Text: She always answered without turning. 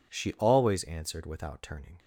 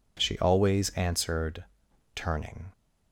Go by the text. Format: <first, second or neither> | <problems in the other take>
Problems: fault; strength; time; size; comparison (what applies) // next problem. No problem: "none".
first | skips "without"; at 1.8 s